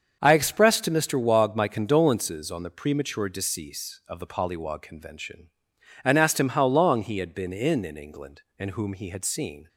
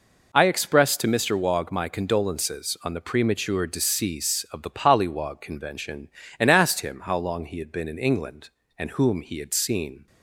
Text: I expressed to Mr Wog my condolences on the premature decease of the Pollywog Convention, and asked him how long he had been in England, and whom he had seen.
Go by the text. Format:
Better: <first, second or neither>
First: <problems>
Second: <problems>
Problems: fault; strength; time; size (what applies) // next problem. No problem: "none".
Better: second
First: starts louder than the rest; until 1.2 s; 7 dB // says "in" twice; at 7.8 s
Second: none